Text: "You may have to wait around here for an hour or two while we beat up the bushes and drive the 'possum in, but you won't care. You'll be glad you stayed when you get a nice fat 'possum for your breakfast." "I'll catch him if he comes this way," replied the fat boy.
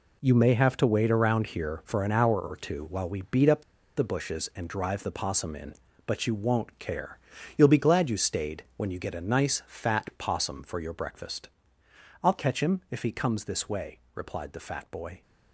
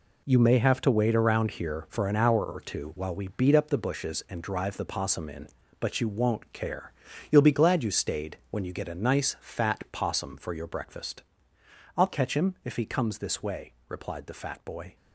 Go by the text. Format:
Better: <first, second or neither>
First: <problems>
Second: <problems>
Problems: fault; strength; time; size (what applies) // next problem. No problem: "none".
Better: second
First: pauses between "up" and "the"; slight; at 3.6 s; 0.35 s long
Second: none